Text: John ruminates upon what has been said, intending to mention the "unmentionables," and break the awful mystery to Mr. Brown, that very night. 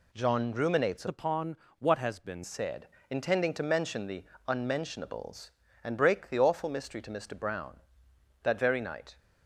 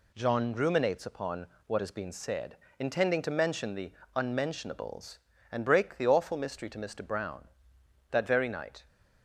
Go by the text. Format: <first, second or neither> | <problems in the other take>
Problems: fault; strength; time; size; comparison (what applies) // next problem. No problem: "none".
second | changes voice from "upon" to "been"; from 1.0 to 2.4 s; 1.4 s long // pauses between "upon" and "what"; slight; at 1.5 s; 0.22 s long; slight in the second // pauses between "the" and "unmentionables"; slight; at 4.2 s; 0.24 s long; slight in the second